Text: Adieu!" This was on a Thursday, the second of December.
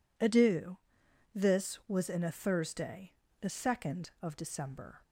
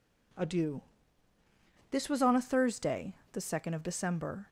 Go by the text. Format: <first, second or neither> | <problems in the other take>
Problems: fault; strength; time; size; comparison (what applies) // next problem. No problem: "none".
second | says "in" for "on"; at 2.0 s